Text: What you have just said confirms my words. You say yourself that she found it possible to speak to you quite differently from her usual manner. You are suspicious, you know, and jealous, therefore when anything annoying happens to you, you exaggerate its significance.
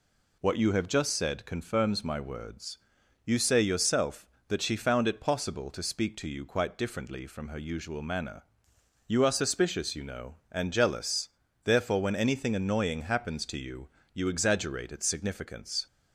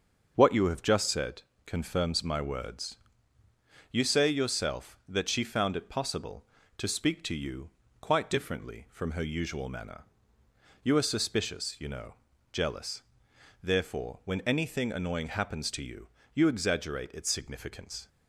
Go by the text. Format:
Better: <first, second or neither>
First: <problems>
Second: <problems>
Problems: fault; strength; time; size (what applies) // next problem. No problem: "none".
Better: first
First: none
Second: starts louder than the rest; until 1.3 s; 6.5 dB // pauses between "said" and "confirms"; slight; at 1.4 s; 0.20 s long // pauses between "you" and "quite"; slight; at 7.6 s; 0.32 s long // skips "and"; at 12.3 s